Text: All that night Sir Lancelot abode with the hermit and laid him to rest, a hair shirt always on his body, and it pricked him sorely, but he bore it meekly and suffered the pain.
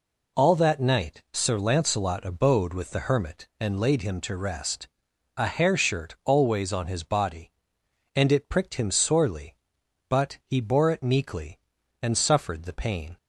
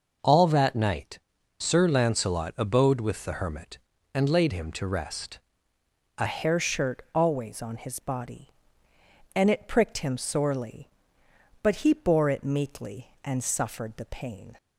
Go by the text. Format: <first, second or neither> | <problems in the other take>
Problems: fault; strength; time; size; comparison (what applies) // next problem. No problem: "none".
first | pauses between "night" and "Sir"; at 1.1 s; 0.42 s long // changes voice at "hair"; from 6.2 s on; 8.3 s long